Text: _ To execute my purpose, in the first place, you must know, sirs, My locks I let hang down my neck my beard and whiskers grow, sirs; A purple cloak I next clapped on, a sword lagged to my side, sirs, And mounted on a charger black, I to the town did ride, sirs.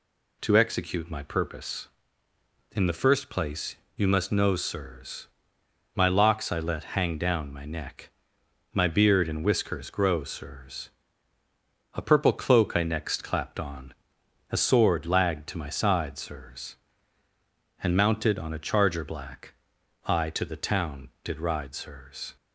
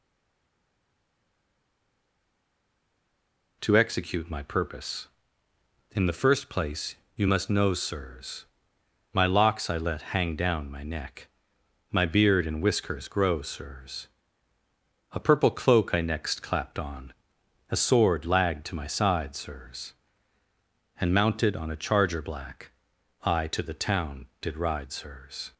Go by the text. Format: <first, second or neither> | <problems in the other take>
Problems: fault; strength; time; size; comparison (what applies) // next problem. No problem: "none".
first | stays silent before the first word; strong; until 3.6 s; 3.6 s long // pauses between "neck" and "my"; noticeable; at 11.2 s; 0.62 s long; noticeable in the first